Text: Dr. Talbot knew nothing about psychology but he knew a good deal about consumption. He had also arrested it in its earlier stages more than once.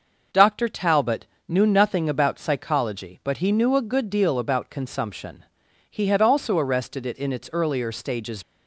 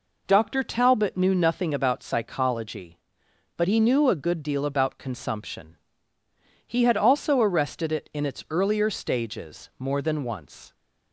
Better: second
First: pauses between "Talbot" and "knew"; slight; at 1.2 s; 0.22 s long // stops before "more than once"; at 8.4 s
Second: none

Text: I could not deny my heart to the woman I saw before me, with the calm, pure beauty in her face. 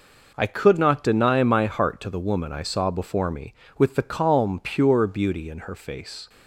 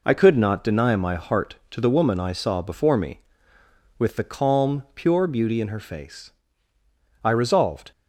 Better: first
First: none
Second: goes on to say "I resolved"; noticeable; from 7.2 s on; 0.68 s long

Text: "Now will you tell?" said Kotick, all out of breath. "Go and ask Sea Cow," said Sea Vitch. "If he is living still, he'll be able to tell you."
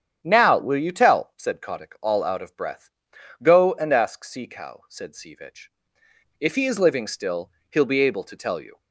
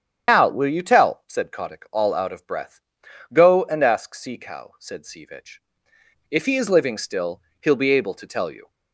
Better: first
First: starts louder than the rest; strong; until 1.2 s; 9 dB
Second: loses the start of "Now"; at 0.2 s; 145 ms // starts louder than the rest; strong; until 1.3 s; 8.5 dB

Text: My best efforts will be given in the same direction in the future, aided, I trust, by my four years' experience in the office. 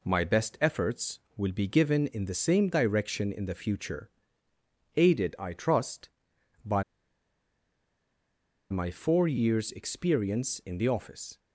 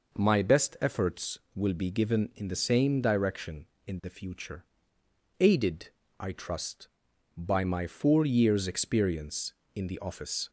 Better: second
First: pauses between "by" and "my"; strong; at 6.8 s; 1.8 s long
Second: none

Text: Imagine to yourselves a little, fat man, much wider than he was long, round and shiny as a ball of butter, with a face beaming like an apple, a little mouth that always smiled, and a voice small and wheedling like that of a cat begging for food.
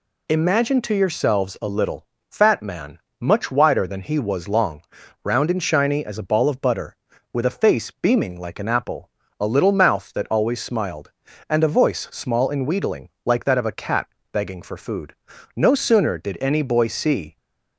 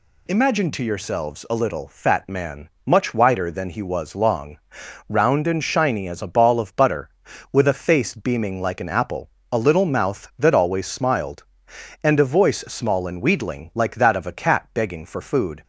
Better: second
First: pauses between "wheedling" and "like"; slight; at 13.1 s; 0.16 s long // pauses between "cat" and "begging"; slight; at 14.0 s; 0.26 s long // goes on to say "No sooner did any boy see"; strong; from 15.5 s on; 1.8 s long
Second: none

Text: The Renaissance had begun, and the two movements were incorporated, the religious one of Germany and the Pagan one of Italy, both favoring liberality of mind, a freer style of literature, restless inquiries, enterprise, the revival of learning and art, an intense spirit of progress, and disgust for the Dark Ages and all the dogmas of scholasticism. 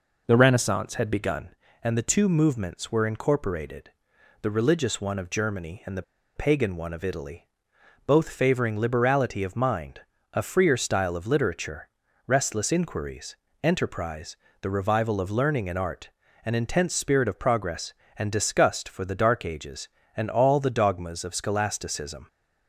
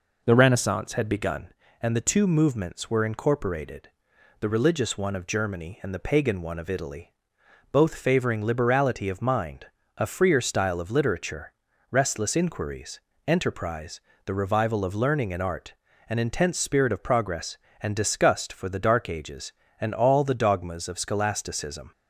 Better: second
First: pauses between "the" and "Pagan"; slight; at 6.0 s; 0.34 s long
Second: none

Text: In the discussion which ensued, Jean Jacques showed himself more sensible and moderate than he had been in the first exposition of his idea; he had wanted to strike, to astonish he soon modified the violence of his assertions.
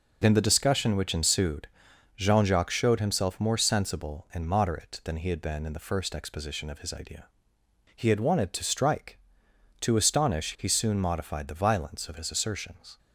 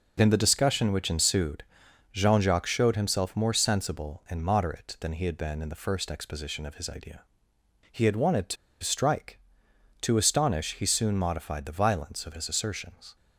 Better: first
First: none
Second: pauses between "to" and "strike"; slight; at 8.5 s; 0.27 s long

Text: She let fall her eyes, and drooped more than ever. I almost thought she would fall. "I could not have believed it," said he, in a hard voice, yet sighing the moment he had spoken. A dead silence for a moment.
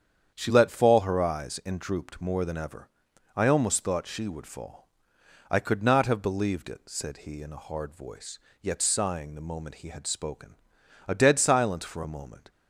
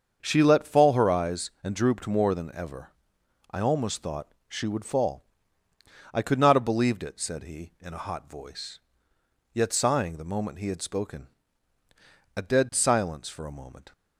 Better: first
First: starts louder than the rest; strong; until 1.3 s; 8 dB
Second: starts louder than the rest; until 1.2 s; 7 dB // says "hot" for "hard"; at 8.0 s

